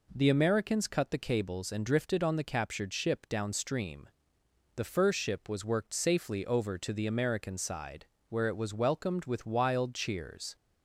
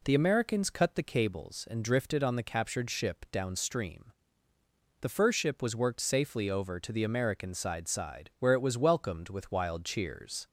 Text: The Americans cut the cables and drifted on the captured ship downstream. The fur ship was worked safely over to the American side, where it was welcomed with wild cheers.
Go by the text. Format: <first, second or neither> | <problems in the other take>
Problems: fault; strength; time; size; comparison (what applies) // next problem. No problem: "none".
first | says "side" twice; at 7.8 s